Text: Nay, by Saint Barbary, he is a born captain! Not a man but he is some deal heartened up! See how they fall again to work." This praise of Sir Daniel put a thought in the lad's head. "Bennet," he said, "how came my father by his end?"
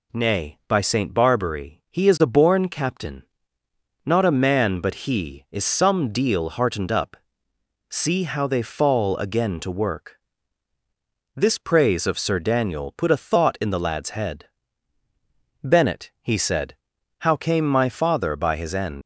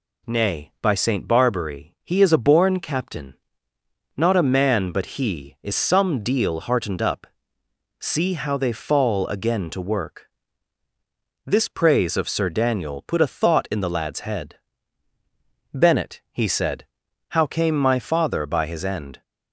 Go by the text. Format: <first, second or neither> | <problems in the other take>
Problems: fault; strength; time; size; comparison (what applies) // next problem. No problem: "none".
second | leaves "end" unfinished; at 19.0 s; 105 ms